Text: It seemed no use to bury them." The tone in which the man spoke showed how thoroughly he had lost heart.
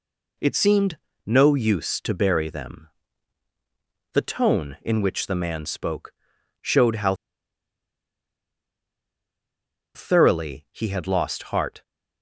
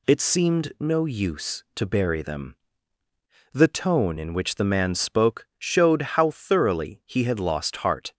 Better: second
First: pauses between "seemed" and "no"; slight; at 0.9 s; 0.28 s long // pauses between "spoke" and "showed"; noticeable; at 6.1 s; 0.48 s long // pauses between "how" and "thoroughly"; strong; at 7.1 s; 2.7 s long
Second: none

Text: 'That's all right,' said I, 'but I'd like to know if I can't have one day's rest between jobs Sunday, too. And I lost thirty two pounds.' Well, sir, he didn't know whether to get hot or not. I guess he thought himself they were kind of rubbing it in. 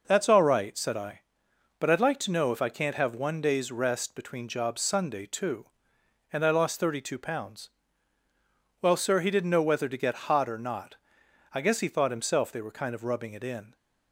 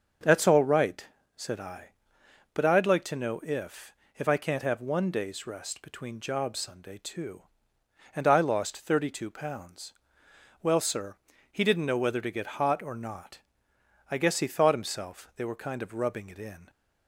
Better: first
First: none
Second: starts louder than the rest; until 1.5 s; 6.5 dB // says "if" twice; at 4.1 s

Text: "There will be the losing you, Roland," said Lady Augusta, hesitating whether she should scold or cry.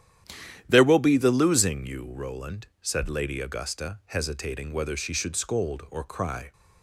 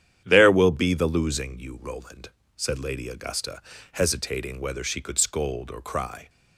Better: first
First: starts louder than the rest; strong; until 1.6 s; 10.5 dB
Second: starts louder than the rest; strong; until 1.2 s; 9.5 dB // says "could" for "should"; at 5.0 s

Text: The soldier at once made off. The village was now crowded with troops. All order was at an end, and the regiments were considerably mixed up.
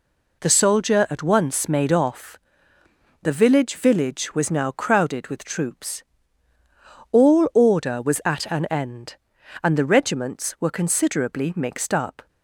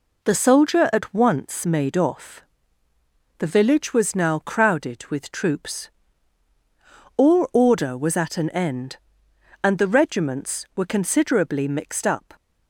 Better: second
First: says "village" twice; at 3.7 s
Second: none

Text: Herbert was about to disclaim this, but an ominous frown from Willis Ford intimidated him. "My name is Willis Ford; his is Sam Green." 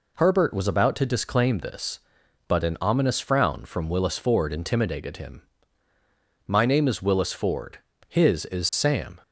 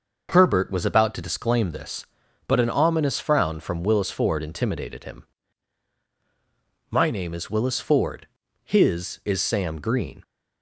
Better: second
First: stops before "Green"; at 9.2 s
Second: none

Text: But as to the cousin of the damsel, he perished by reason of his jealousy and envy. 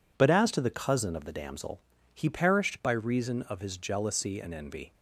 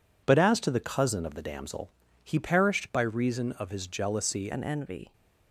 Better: first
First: none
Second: changes voice at "and"; from 4.5 s on; 0.6 s long

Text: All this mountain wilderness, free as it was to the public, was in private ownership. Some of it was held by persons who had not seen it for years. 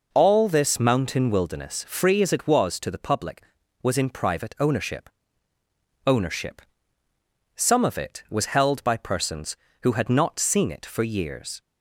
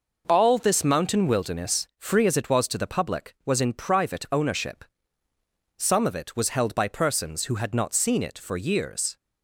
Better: second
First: says "ownership" twice; at 6.0 s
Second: none

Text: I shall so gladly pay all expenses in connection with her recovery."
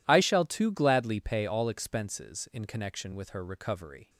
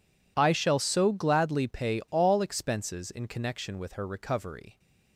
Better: second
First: says "too" for "so"; at 0.4 s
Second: none

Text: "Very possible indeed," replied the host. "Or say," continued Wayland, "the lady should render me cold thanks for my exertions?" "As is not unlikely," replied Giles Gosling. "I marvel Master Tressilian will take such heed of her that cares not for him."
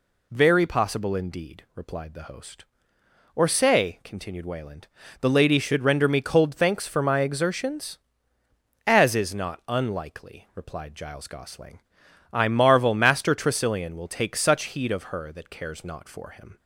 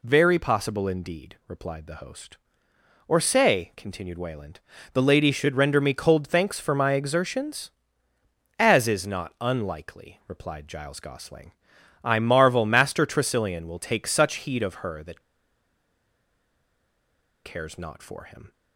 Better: first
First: none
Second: pauses between "that" and "cares"; strong; at 15.2 s; 2.2 s long

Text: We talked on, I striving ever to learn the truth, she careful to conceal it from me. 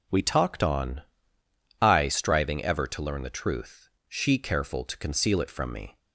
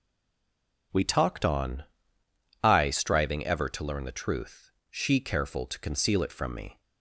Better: first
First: none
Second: stays silent before the first word; slight; until 0.9 s; 0.9 s long

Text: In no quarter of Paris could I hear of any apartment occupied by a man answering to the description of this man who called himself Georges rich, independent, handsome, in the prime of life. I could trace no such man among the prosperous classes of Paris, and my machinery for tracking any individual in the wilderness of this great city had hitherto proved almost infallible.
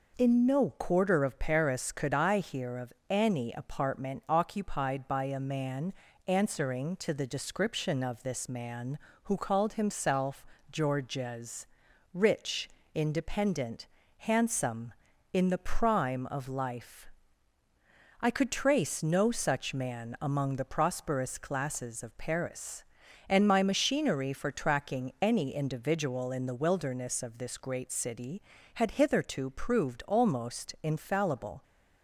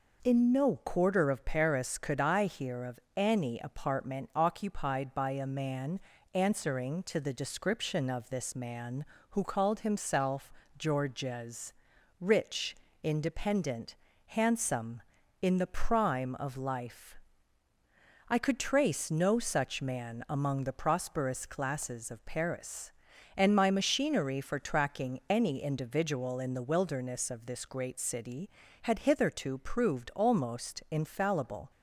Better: neither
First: pauses between "of" and "any"; slight; at 2.9 s; 0.18 s long // pauses between "man" and "answering"; slight; at 5.9 s; 0.36 s long // pauses between "himself" and "Georges"; slight; at 10.4 s; 0.26 s long // pauses between "Georges" and "rich"; noticeable; at 11.6 s; 0.46 s long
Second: pauses between "of" and "any"; slight; at 2.9 s; 0.18 s long // pauses between "man" and "answering"; slight; at 5.9 s; 0.36 s long // pauses between "himself" and "Georges"; slight; at 10.5 s; 0.26 s long // pauses between "Georges" and "rich"; noticeable; at 11.7 s; 0.46 s long

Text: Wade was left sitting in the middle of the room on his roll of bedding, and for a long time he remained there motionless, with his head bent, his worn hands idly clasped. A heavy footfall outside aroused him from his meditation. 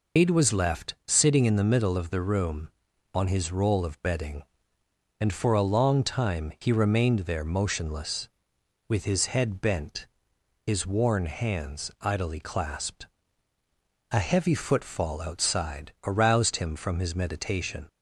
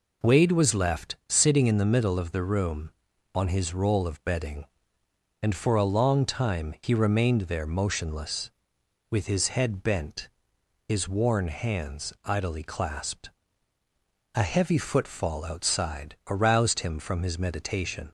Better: second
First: loses the start of "Wade"; at 0.1 s; 140 ms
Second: none

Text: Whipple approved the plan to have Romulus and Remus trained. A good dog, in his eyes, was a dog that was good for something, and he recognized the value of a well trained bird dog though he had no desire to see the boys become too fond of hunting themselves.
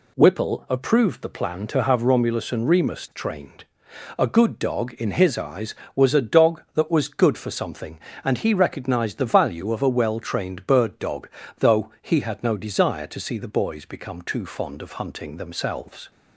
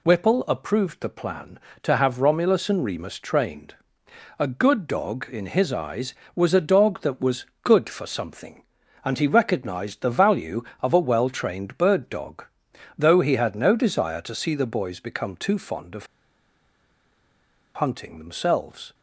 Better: first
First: pauses between "dog" and "though"; slight; at 11.2 s; 0.30 s long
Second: pauses between "was" and "good"; slight; at 7.4 s; 0.18 s long // pauses between "dog" and "though"; noticeable; at 12.4 s; 0.52 s long // pauses between "of" and "hunting"; strong; at 16.0 s; 1.6 s long

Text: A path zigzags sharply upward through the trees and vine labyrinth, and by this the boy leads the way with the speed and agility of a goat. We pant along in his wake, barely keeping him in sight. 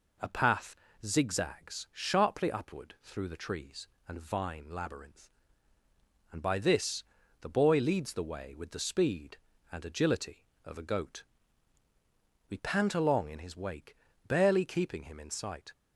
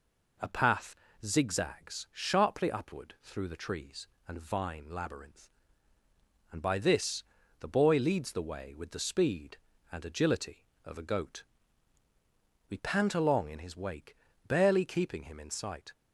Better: neither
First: pauses between "path" and "zigzags"; slight; at 0.7 s; 0.30 s long // pauses between "this" and "the"; slight; at 7.0 s; 0.36 s long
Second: pauses between "path" and "zigzags"; slight; at 0.9 s; 0.30 s long // pauses between "this" and "the"; slight; at 7.2 s; 0.35 s long

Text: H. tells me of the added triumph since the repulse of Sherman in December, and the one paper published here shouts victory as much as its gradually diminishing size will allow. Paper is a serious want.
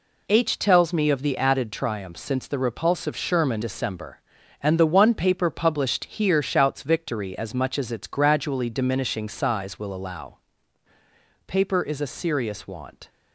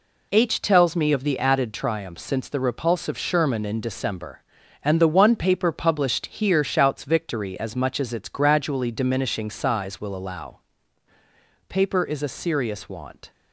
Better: second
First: skips "in"; at 3.6 s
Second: none

